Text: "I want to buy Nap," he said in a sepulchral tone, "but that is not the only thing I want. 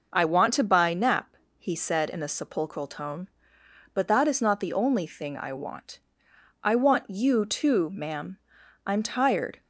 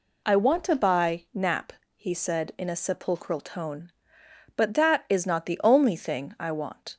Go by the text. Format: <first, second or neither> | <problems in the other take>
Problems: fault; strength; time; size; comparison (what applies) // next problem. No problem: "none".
second | goes on to say "I want you too ma'am I'm tired"; strong; from 6.6 s on; 2.9 s long